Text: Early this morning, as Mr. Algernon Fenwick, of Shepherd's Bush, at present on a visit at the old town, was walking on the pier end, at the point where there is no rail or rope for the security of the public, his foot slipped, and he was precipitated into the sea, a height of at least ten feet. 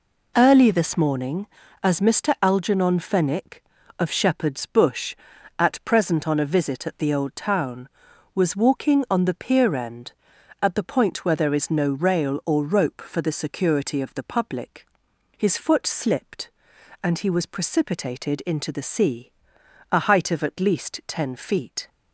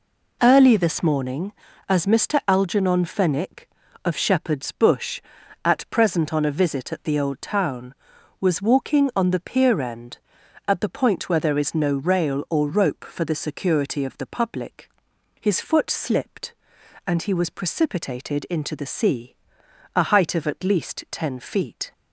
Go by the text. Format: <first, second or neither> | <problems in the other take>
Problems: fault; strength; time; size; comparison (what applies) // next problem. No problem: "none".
neither | none